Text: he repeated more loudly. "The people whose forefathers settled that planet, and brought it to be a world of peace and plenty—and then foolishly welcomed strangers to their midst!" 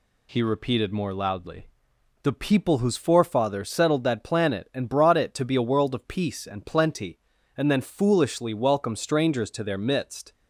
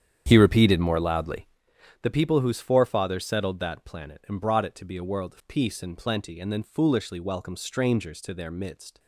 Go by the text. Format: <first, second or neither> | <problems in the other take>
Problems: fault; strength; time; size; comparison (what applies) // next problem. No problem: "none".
first | starts louder than the rest; strong; until 1.6 s; 9 dB